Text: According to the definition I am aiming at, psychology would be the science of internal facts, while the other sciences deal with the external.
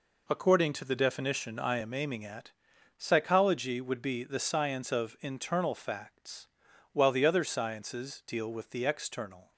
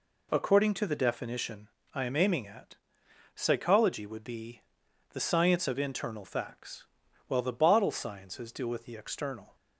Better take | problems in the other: first | pauses between "definition" and "I"; slight; at 1.6 s; 0.24 s long // pauses between "be" and "the"; noticeable; at 4.6 s; 0.52 s long // says "bottle" for "other"; at 7.5 s

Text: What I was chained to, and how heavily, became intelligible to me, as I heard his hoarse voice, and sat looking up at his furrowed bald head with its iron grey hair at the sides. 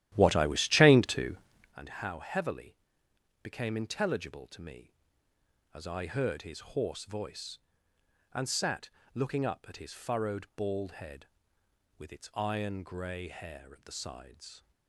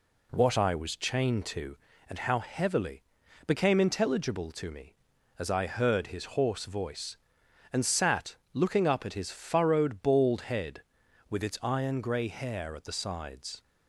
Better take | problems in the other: second | starts louder than the rest; strong; until 1.8 s; 13 dB // pauses between "sat" and "looking"; slight; at 8.9 s; 0.24 s long; slight in the second

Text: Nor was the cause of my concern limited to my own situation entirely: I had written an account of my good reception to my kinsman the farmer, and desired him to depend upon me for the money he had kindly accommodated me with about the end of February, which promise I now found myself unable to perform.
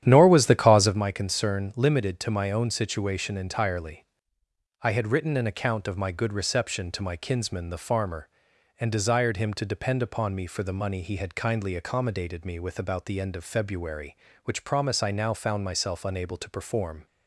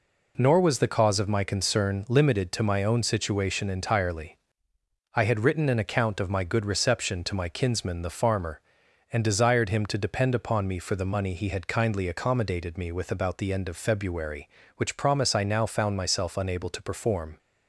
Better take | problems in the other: second | starts louder than the rest; strong; until 1.0 s; 10.5 dB

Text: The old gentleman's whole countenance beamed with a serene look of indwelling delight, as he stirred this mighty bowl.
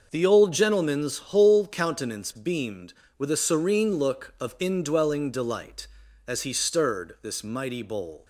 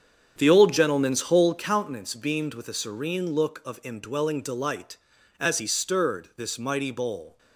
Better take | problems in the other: first | starts louder than the rest; strong; until 1.6 s; 7.5 dB

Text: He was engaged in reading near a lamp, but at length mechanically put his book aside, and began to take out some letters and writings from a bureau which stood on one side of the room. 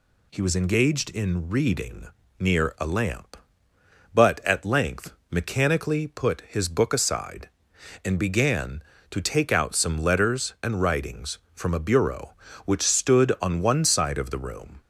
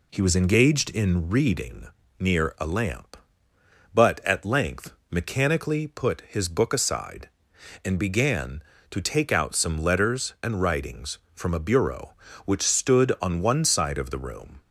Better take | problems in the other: first | starts louder than the rest; slight; until 1.6 s; 2.5 dB // pauses between "reading" and "near"; slight; at 1.8 s; 0.32 s long; slight in the first // pauses between "length" and "mechanically"; slight; at 4.9 s; 0.16 s long; slight in the first

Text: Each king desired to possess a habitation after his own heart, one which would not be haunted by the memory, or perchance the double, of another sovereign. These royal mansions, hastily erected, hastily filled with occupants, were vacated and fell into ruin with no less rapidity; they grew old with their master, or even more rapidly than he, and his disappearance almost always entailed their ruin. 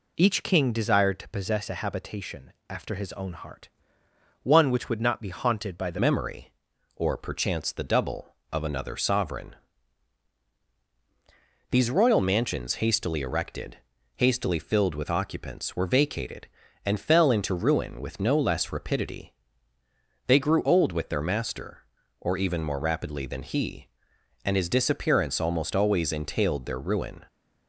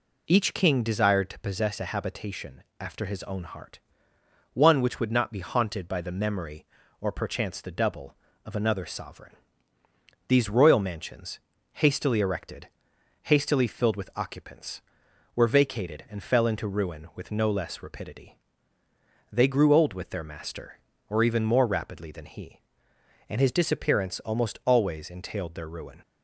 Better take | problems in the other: second | pauses between "habitation" and "after"; slight; at 2.5 s; 0.18 s long; slight in the second // changes voice at "memory"; from 6.0 s on; 21.2 s long

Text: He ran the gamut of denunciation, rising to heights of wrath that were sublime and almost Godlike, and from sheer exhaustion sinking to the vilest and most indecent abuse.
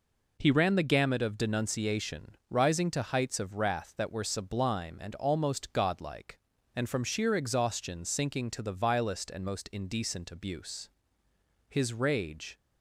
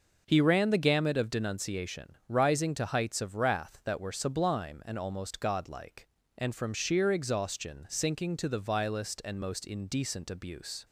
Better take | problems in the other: second | goes on to say "His rage"; noticeable; from 11.6 s on; 0.88 s long

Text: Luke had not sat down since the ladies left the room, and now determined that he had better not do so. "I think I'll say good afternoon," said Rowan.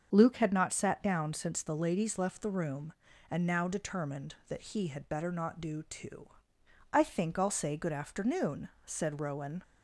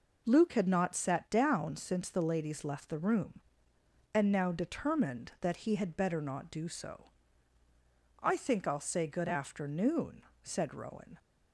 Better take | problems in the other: second | starts louder than the rest; until 1.1 s; 6.5 dB // says "too" for "so"; at 5.8 s

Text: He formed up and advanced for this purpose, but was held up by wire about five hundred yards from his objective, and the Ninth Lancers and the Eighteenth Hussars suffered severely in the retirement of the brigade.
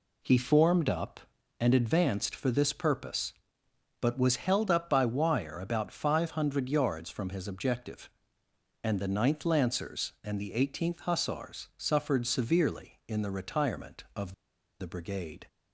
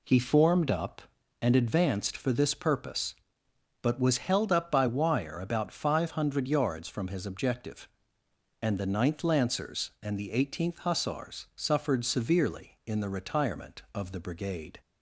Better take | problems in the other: second | pauses between "of" and "the"; noticeable; at 14.3 s; 0.47 s long

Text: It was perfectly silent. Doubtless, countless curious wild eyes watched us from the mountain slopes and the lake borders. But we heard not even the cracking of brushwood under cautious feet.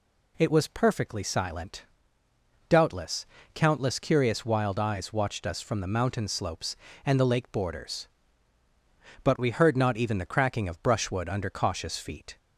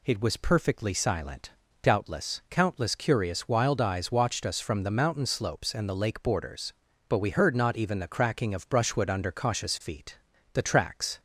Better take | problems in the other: first | goes on to say "The tracks"; noticeable; from 10.5 s on; 0.68 s long

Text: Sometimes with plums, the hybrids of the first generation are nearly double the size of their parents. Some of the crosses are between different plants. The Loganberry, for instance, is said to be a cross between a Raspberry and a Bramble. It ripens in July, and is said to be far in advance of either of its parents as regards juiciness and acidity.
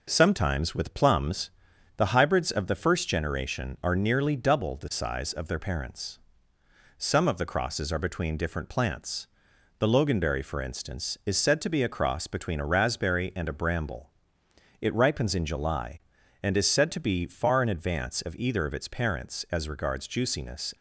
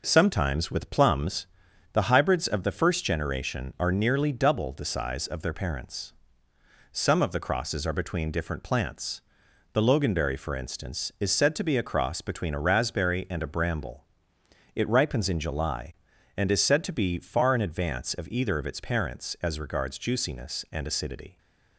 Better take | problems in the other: second | stops before "and acidity"; at 20.7 s

